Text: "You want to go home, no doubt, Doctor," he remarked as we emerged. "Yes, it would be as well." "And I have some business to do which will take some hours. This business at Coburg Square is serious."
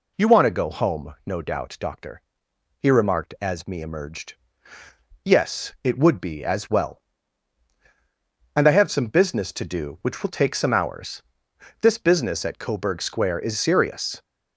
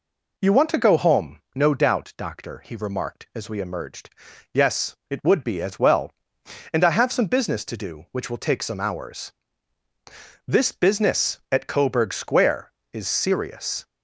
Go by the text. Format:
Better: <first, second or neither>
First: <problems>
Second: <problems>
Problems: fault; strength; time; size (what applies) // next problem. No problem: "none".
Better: second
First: says "me" for "we"; at 3.6 s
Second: none